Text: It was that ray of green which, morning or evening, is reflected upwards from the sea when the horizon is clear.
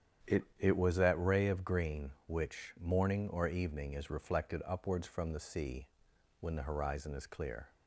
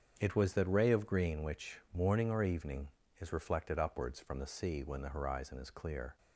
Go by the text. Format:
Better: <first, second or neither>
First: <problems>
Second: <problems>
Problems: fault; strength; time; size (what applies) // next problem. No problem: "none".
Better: second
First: starts louder than the rest; strong; until 1.4 s; 9 dB // says "It" twice; at 0.5 s // pauses between "sea" and "when"; noticeable; at 5.8 s; 0.52 s long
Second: starts louder than the rest; strong; until 1.2 s; 7.5 dB